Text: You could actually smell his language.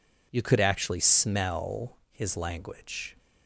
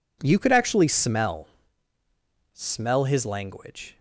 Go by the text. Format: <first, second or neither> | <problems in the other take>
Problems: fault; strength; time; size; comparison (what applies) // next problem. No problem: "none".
first | says "smell" twice; at 2.5 s